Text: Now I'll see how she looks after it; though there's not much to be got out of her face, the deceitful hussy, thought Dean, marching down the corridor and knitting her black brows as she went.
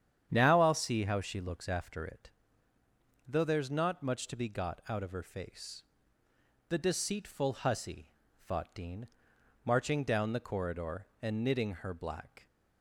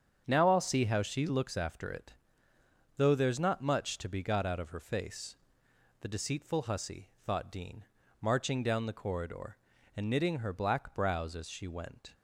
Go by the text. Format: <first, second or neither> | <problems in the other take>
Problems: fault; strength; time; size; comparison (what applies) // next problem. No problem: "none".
second | starts louder than the rest; strong; until 1.3 s; 9 dB; strong in the second // stops before "brows as she went"; at 12.4 s